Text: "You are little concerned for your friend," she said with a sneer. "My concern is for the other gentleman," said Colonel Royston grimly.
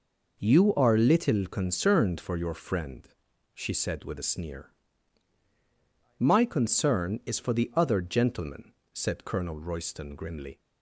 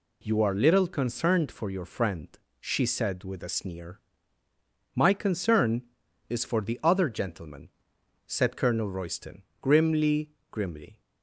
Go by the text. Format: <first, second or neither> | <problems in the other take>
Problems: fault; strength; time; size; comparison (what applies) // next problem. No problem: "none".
first | pauses between "Royston" and "grimly"; slight; at 9.4 s; 0.18 s long // says "grimly" twice; at 10.5 s